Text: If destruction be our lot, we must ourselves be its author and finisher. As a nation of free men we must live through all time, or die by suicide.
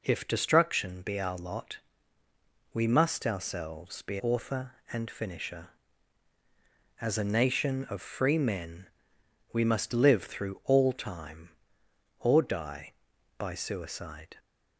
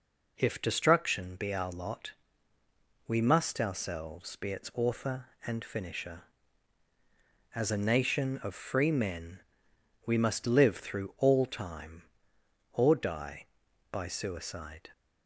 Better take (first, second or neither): second